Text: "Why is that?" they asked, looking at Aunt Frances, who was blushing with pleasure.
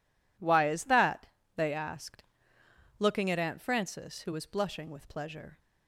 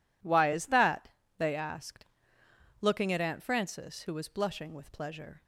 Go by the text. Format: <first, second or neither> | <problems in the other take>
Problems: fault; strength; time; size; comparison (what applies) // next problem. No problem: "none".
neither | none